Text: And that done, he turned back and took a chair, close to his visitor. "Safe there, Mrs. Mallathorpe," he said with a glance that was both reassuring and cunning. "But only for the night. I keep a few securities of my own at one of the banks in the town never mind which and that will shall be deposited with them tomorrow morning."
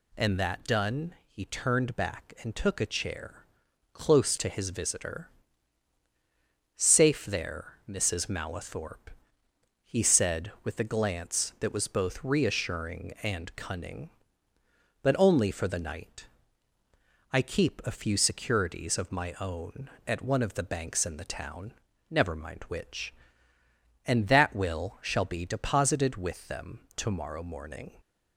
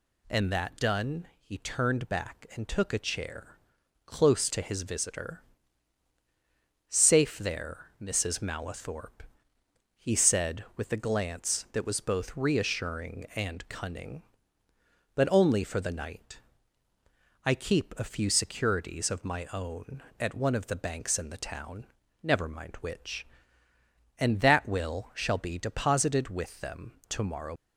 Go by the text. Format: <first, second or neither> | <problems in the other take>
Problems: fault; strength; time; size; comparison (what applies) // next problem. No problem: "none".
first | pauses between "town" and "never"; at 21.8 s; 0.38 s long; also in the first // pauses between "them" and "tomorrow"; slight; at 26.9 s; 0.16 s long; slight in the first // stops before "morning"; at 27.5 s